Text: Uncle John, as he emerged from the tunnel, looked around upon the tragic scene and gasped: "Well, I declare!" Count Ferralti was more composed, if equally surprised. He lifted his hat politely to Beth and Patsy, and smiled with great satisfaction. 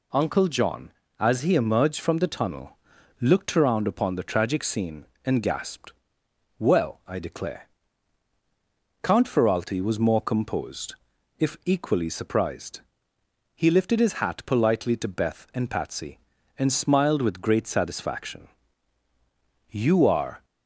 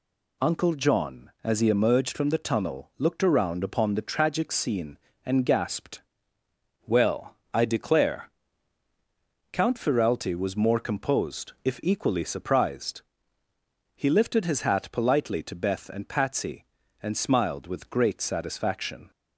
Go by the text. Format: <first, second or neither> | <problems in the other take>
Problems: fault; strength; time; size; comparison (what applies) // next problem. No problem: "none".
second | goes on to say "You are"; noticeable; from 19.7 s on; 0.74 s long